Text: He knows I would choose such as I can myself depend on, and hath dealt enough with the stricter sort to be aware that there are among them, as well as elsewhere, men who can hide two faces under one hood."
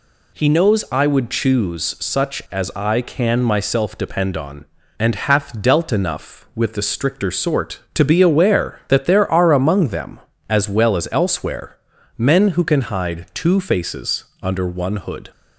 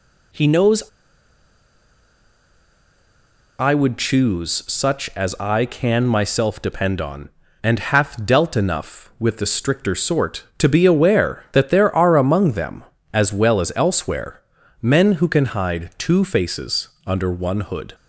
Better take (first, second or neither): first